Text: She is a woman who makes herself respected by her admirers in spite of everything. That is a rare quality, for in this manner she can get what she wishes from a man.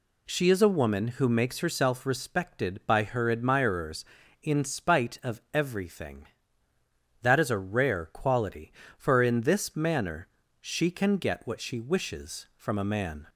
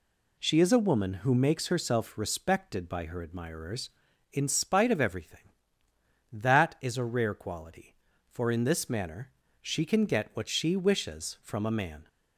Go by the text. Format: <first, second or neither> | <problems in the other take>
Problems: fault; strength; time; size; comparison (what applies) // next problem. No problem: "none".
neither | pauses between "manner" and "she"; slight; the same in both